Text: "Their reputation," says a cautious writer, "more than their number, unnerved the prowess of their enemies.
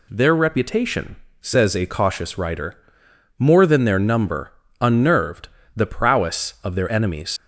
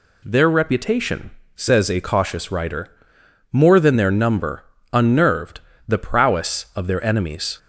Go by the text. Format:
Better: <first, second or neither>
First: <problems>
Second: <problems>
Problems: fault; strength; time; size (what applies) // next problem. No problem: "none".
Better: second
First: pauses between "unnerved" and "the"; slight; at 5.4 s; 0.26 s long // leaves "enemies" unfinished; at 7.3 s; 80 ms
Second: pauses between "unnerved" and "the"; slight; at 5.6 s; 0.26 s long